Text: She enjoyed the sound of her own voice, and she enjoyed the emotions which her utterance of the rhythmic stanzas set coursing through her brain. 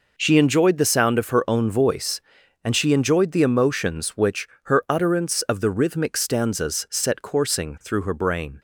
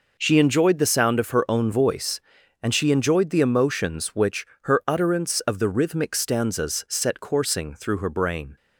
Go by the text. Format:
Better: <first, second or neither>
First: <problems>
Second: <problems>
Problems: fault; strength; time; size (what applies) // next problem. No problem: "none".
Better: neither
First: pauses between "which" and "her"; slight; at 4.4 s; 0.16 s long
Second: pauses between "which" and "her"; slight; at 4.4 s; 0.16 s long